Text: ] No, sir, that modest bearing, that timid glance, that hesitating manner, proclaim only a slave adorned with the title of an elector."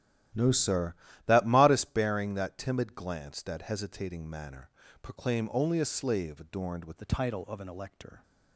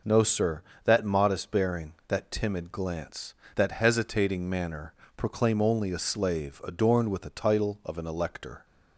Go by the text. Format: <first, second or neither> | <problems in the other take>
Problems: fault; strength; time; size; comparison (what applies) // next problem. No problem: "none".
second | starts louder than the rest; strong; until 1.6 s; 13 dB // changes voice at "the"; from 6.9 s on; 1.3 s long